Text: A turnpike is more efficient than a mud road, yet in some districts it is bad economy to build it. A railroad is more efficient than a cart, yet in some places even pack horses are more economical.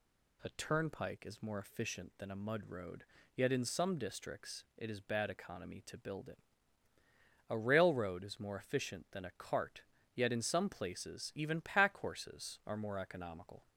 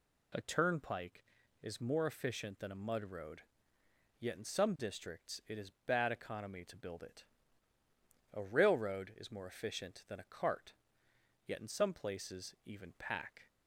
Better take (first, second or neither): first